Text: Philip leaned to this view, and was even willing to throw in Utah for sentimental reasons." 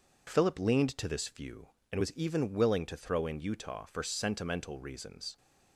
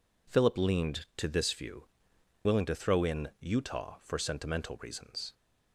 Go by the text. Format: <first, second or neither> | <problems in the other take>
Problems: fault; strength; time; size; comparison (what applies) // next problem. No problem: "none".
first | skips "and was even"; at 2.1 s